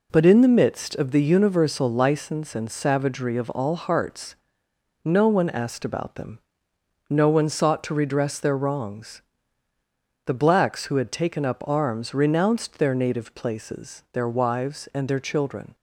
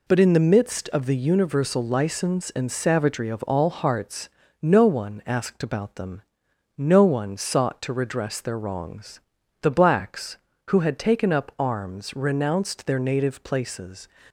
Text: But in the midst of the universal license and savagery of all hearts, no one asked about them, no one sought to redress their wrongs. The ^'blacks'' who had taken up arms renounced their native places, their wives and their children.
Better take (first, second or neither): first